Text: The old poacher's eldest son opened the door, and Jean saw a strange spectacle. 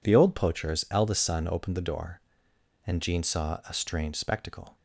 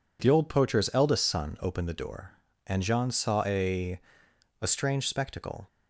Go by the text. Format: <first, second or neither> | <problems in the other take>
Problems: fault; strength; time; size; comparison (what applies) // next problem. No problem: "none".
first | says "a" twice; at 4.6 s